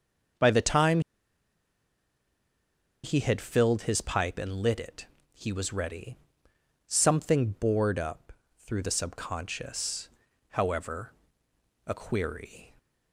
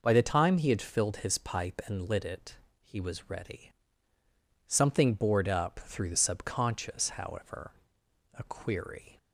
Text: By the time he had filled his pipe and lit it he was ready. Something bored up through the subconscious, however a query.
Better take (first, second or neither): second